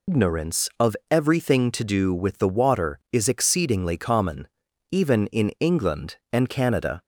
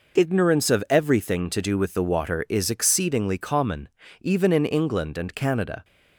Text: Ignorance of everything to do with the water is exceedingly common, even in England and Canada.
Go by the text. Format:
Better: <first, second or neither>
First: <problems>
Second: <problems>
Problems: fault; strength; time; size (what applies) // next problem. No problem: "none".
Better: second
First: loses the start of "Ignorance"; at 0.0 s; 165 ms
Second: none